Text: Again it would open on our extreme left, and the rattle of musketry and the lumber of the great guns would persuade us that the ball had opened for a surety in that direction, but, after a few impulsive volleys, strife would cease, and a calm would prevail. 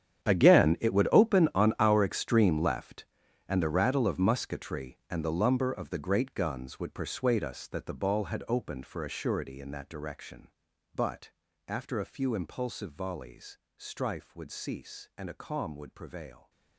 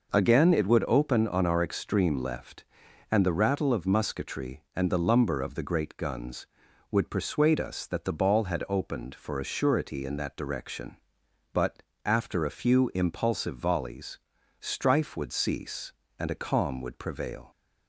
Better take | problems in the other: second | gets quieter; strong; throughout; 17 dB

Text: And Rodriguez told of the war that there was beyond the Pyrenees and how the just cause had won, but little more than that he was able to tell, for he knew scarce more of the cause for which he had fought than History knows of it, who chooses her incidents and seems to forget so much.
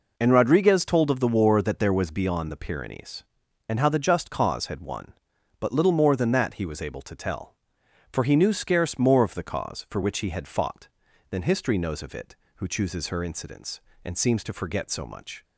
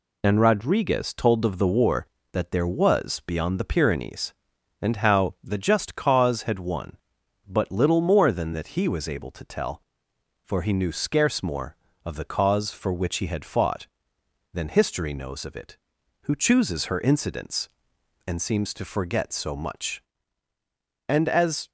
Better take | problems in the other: first | goes on to say "And as"; noticeable; from 21.0 s on; 0.62 s long

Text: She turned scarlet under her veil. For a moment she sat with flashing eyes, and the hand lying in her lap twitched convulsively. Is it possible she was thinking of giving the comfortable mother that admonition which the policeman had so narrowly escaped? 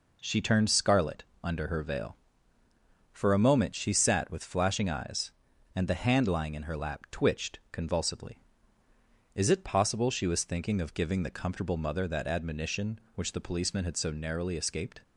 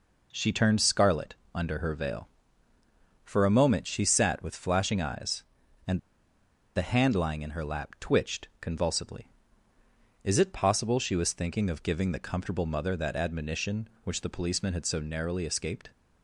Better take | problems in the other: first | pauses between "scarlet" and "under"; slight; at 1.3 s; 0.18 s long; slight in the first // pauses between "and" and "the"; noticeable; at 5.9 s; 0.76 s long

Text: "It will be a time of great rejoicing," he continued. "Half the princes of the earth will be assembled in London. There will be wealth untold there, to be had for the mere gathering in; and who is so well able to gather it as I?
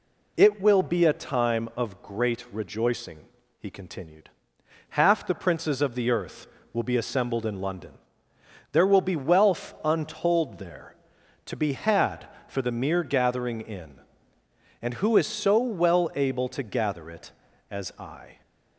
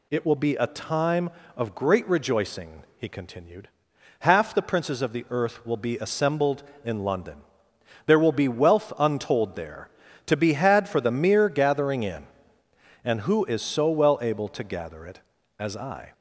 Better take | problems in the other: first | gets louder; slight; throughout; 2.5 dB

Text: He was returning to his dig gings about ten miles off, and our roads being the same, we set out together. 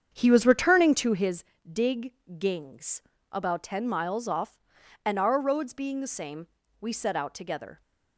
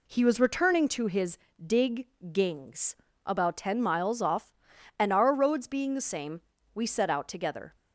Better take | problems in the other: second | starts louder than the rest; strong; until 1.4 s; 8 dB // pauses between "his" and "dig"; slight; at 1.4 s; 0.28 s long; slight in the second // pauses between "dig" and "gings"; slight; at 2.1 s; 0.24 s long; slight in the second // pauses between "gings" and "about"; slight; at 3.0 s; 0.30 s long; slight in the second

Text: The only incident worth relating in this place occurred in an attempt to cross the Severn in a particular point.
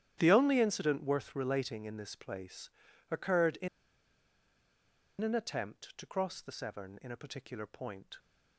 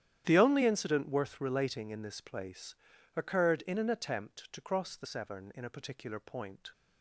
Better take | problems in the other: second | starts louder than the rest; strong; until 1.1 s; 11 dB; strong in the second // pauses between "place" and "occurred"; at 2.6 s; 0.40 s long; also in the second // pauses between "in" and "an"; strong; at 3.6 s; 1.5 s long

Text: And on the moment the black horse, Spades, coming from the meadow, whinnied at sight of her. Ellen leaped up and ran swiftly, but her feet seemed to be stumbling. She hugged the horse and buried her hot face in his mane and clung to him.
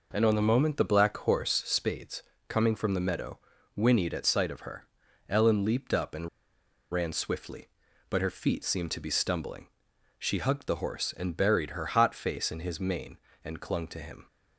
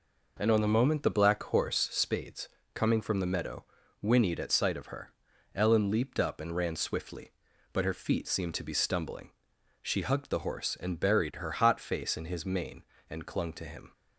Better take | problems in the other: second | pauses between "and" and "ran"; noticeable; at 6.2 s; 0.63 s long

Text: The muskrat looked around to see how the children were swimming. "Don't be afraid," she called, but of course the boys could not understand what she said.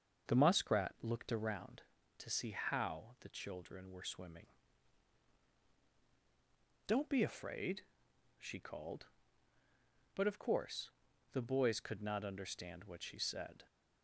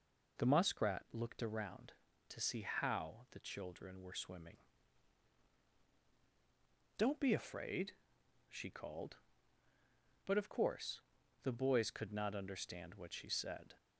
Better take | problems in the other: second | starts louder than the rest; until 1.8 s; 6.5 dB // pauses between "course" and "the"; at 10.8 s; 0.42 s long; also in the second

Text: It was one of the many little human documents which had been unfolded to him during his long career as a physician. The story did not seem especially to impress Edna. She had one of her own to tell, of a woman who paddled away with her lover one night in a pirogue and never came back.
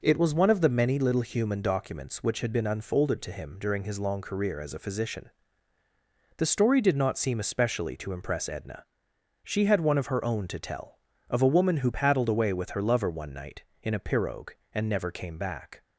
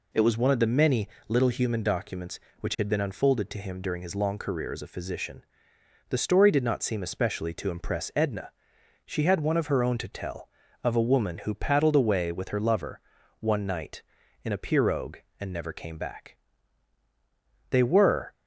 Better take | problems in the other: first | pauses between "many" and "little"; slight; at 1.0 s; 0.18 s long // pauses between "lover" and "one"; at 12.9 s; 0.40 s long // goes on to say "They were"; noticeable; from 17.6 s on; 0.62 s long

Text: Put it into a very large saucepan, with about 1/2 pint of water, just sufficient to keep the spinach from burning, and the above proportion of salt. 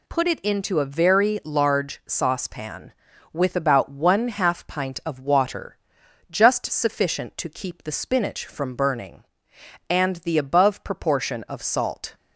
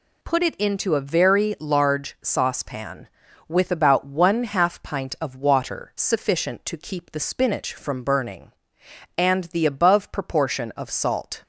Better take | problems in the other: first | skips "just"; at 5.9 s

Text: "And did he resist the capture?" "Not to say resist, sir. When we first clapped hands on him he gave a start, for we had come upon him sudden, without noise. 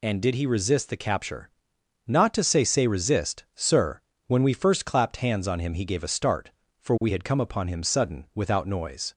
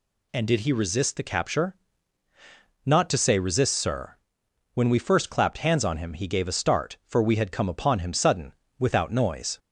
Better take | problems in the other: second | says "say" twice; at 2.6 s

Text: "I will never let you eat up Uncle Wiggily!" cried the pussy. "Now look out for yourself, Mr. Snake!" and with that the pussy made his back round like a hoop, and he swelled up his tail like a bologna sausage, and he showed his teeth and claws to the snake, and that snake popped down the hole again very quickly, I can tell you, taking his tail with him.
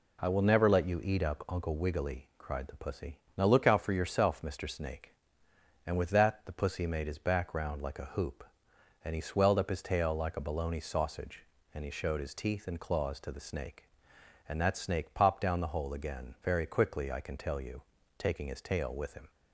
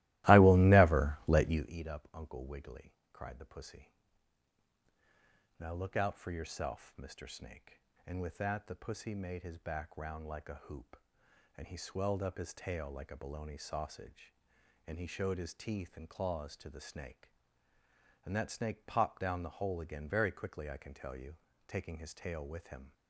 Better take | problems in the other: first | starts louder than the rest; strong; until 1.7 s; 17.5 dB

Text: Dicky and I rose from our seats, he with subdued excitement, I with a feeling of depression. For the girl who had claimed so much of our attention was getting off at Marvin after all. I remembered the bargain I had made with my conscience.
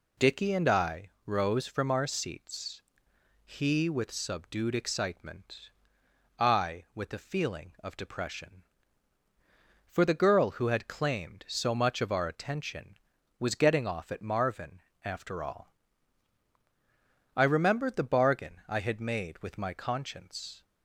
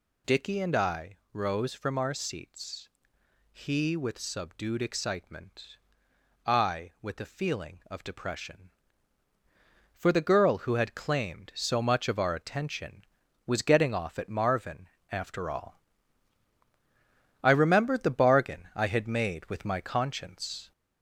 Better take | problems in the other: first | gets louder; slight; throughout; 3 dB // pauses between "I" and "rose"; slight; at 1.1 s; 0.16 s long; slight in the first // pauses between "Marvin" and "after"; slight; at 14.8 s; 0.24 s long; slight in the first

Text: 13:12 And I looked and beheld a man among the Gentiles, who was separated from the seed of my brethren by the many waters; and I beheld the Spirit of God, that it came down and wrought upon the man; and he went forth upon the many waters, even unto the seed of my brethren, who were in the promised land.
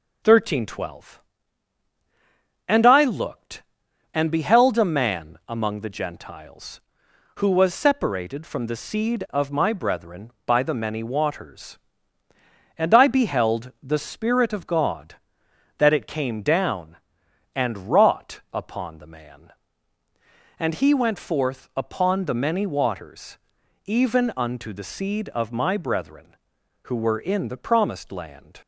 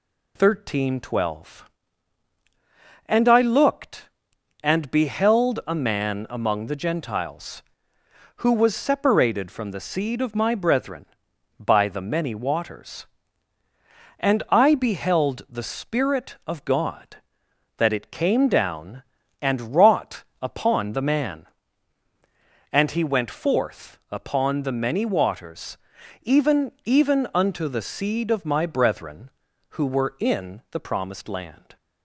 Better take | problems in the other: first | pauses between "wrought" and "upon"; slight; at 20.2 s; 0.20 s long // says "even" twice; at 26.8 s

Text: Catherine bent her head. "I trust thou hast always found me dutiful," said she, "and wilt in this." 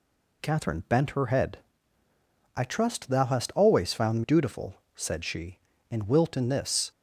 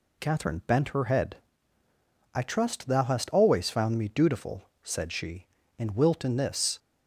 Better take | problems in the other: second | skips "me"; at 4.2 s

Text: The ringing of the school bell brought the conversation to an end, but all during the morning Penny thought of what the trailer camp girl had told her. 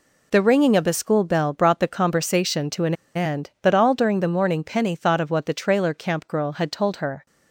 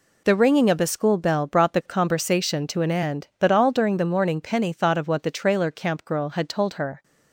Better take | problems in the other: second | pauses between "an" and "end"; slight; at 2.9 s; 0.20 s long

